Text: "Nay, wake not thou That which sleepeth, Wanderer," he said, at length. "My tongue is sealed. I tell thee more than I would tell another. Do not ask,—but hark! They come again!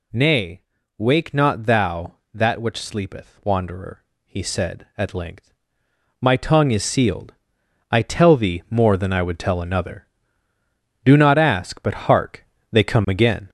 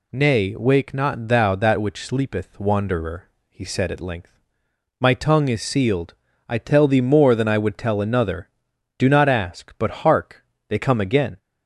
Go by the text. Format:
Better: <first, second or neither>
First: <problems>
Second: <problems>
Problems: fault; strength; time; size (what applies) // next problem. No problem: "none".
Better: second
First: gets louder; noticeable; throughout; 5 dB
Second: none